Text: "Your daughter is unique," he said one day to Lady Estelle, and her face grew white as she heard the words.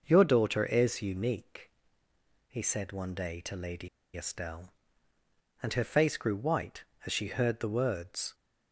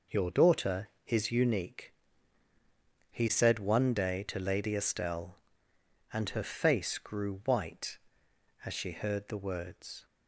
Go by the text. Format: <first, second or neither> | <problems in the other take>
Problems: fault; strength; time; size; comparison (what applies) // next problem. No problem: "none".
second | pauses between "Lady" and "Estelle"; slight; at 3.8 s; 0.27 s long